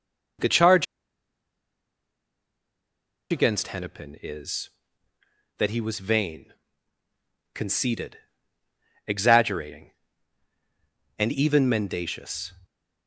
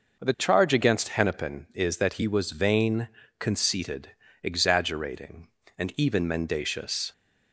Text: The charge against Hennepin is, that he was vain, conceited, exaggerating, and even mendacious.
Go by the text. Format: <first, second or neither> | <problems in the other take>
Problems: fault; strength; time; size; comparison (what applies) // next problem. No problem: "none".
second | pauses between "charge" and "against"; strong; at 0.8 s; 2.4 s long